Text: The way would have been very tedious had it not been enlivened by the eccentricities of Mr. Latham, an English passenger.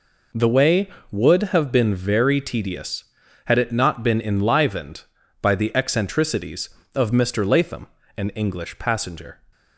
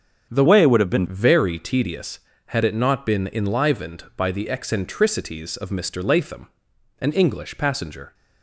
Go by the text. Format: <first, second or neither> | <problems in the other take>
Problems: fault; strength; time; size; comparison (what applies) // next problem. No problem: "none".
first | starts louder than the rest; until 1.3 s; 7 dB // changes voice from "way" to "been"; from 0.4 to 1.0 s; 0.6 s long